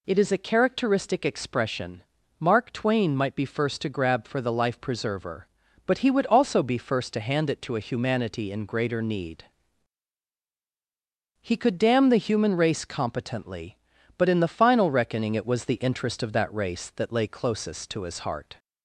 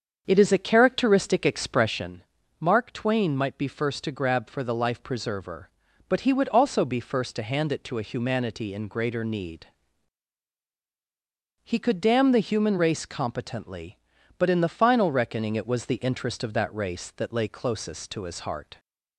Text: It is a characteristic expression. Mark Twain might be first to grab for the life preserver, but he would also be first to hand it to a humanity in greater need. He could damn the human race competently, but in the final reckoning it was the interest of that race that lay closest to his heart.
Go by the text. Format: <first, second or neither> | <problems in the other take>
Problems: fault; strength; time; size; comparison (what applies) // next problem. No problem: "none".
first | starts louder than the rest; until 2.2 s; 7 dB